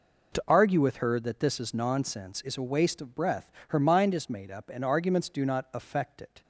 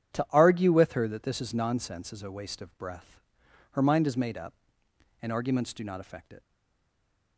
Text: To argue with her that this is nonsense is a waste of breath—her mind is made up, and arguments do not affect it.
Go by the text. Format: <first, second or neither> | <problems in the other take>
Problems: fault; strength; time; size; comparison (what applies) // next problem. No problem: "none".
first | starts louder than the rest; strong; until 1.2 s; 9 dB // stays silent after the last word; from 6.4 s on; 0.9 s long